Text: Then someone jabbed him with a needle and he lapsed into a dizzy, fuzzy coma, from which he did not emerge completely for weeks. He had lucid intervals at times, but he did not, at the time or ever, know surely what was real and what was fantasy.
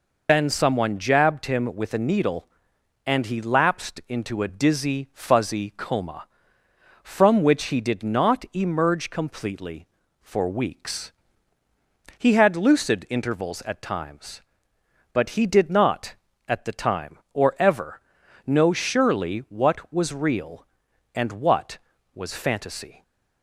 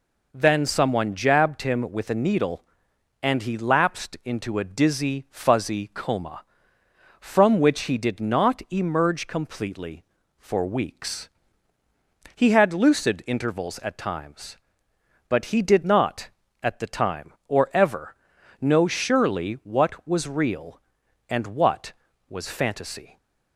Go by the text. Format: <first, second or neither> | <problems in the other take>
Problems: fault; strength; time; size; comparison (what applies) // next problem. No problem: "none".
second | loses the start of "Then"; at 0.2 s; 125 ms